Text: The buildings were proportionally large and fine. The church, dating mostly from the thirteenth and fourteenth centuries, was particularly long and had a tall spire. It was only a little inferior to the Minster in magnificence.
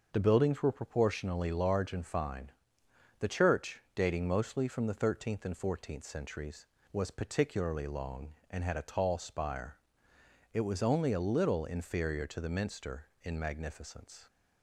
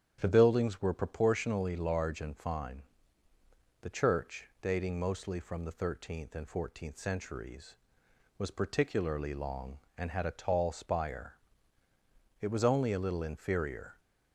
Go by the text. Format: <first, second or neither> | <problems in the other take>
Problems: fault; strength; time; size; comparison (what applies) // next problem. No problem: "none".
first | starts louder than the rest; strong; until 1.2 s; 9 dB; noticeable in the first // stops before "to the Minster in magnificence"; at 13.9 s